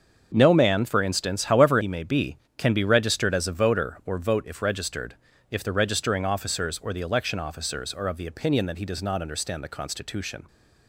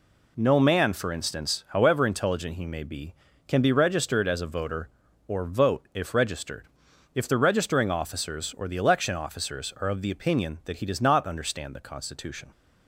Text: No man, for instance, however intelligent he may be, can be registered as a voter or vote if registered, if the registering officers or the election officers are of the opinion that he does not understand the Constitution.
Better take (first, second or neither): second